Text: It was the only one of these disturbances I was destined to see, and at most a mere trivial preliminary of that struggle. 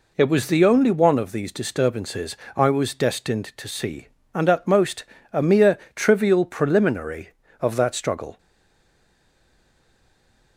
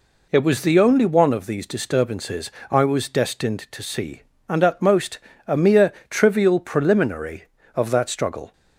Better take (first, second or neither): second